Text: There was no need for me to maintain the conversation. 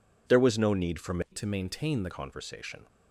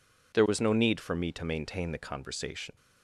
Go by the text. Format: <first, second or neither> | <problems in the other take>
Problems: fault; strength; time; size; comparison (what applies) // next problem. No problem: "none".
second | changes voice from "to" to "the"; from 1.3 to 2.1 s; 0.8 s long